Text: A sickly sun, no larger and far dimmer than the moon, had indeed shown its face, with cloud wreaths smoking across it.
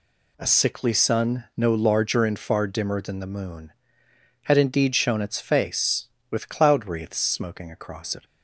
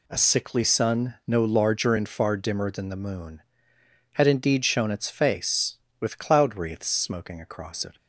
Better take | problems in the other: neither | none

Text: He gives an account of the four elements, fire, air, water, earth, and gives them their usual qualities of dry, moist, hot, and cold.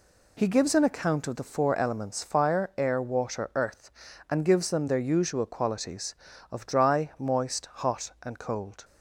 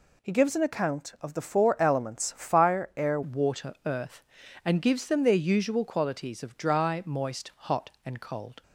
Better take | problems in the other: first | changes voice at "water"; from 3.2 s on; 5.4 s long

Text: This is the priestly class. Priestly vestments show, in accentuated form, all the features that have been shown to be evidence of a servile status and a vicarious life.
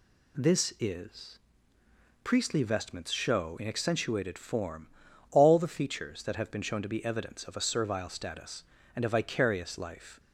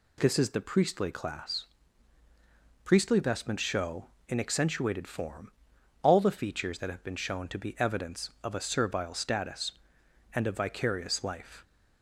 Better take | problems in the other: second | skips "the priestly class"; at 1.7 s

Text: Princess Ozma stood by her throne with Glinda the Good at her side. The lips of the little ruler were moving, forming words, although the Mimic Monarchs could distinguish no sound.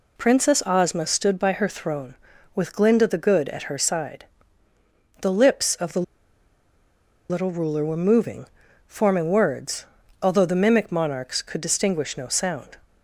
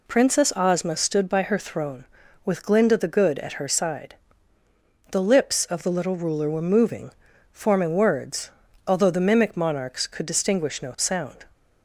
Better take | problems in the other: second | pauses between "the" and "little"; strong; at 6.0 s; 1.2 s long

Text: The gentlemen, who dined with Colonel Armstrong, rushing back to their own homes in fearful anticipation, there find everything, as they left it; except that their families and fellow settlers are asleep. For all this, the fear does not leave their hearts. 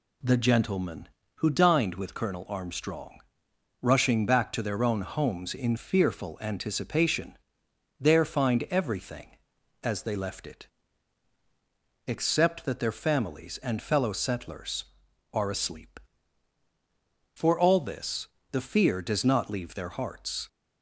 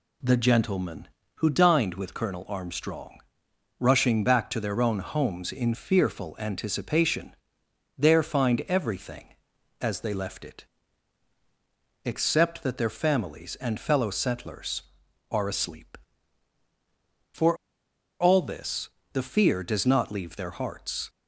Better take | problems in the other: first | pauses between "For" and "all"; noticeable; at 17.5 s; 0.64 s long

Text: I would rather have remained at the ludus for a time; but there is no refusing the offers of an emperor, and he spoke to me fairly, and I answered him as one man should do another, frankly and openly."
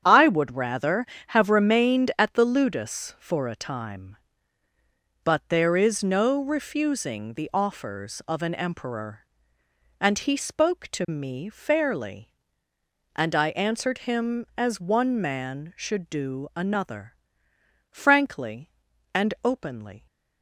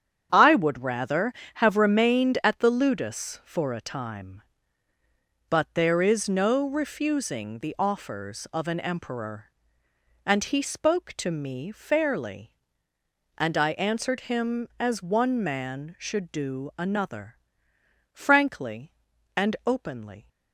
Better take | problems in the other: neither | starts louder than the rest; strong; the same in both

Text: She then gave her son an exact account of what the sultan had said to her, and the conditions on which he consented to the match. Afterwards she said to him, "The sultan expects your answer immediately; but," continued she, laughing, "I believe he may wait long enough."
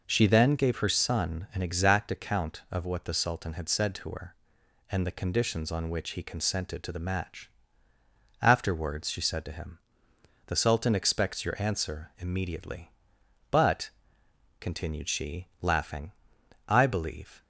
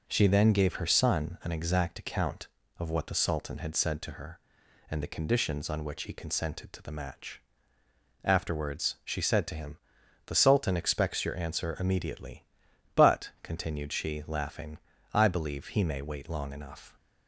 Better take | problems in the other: second | stops before "he may wait long enough"; at 17.4 s

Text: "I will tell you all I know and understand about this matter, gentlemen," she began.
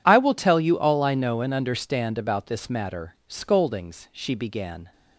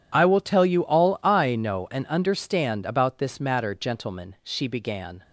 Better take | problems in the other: second | says "scoldings" for "gentlemen"; at 3.2 s

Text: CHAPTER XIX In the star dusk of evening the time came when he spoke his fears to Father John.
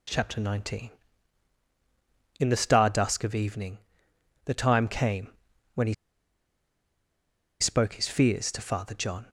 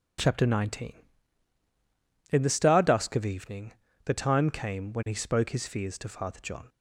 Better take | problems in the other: second | pauses between "evening" and "the"; noticeable; at 3.7 s; 0.70 s long; slight in the second // pauses between "came" and "when"; at 5.3 s; 0.44 s long // pauses between "he" and "spoke"; strong; at 5.9 s; 1.6 s long

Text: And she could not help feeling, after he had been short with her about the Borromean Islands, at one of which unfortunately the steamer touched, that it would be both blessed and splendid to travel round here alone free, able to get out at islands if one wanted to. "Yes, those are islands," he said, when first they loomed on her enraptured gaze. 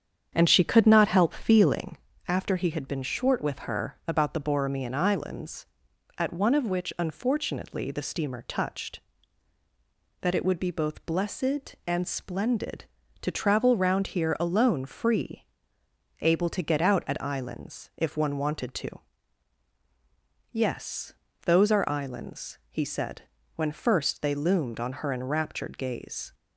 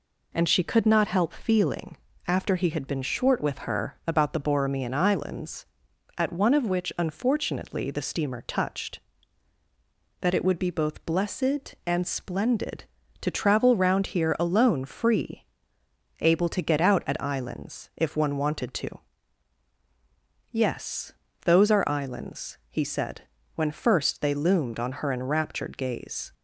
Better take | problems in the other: second | starts louder than the rest; strong; until 2.1 s; 8 dB

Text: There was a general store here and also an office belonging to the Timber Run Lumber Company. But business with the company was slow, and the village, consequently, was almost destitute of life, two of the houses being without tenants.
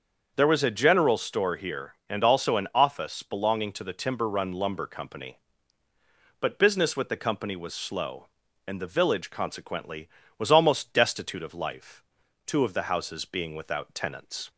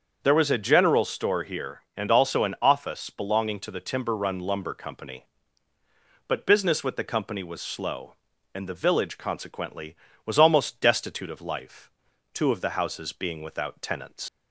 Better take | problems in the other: first | starts louder than the rest; until 1.2 s; 7 dB; also in the first // leaves "tenants" unfinished; at 14.2 s; 90 ms

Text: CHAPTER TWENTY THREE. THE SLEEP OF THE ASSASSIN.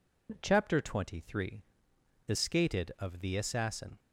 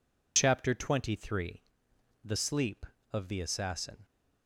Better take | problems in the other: second | says "Skated" for "SLEEP"; at 2.3 s

